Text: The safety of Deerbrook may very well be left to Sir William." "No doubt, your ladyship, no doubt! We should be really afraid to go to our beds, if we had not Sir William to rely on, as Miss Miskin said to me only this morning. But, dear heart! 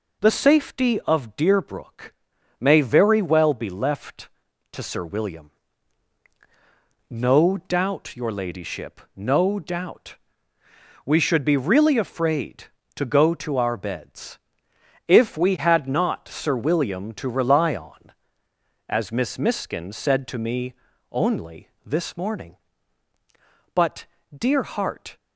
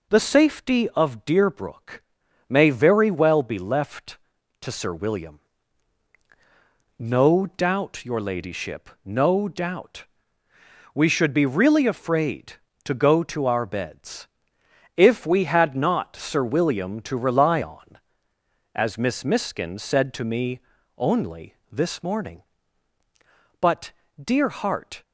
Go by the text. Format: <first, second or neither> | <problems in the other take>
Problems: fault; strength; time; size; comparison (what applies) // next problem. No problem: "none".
neither | pauses between "Deerbrook" and "may"; noticeable; the same in both // pauses between "me" and "only"; slight; the same in both // pauses between "only" and "this"; slight; the same in both